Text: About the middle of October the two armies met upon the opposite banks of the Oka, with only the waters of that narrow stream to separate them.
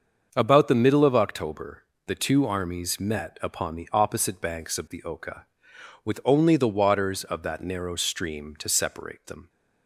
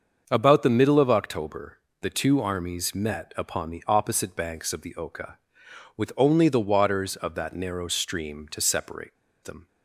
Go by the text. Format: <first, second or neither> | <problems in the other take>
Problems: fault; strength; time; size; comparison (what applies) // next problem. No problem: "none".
first | starts louder than the rest; until 1.3 s; 6.5 dB; also in the first // pauses between "October" and "the"; slight; at 1.7 s; 0.24 s long; slight in the first // pauses between "separate" and "them"; slight; at 9.1 s; 0.28 s long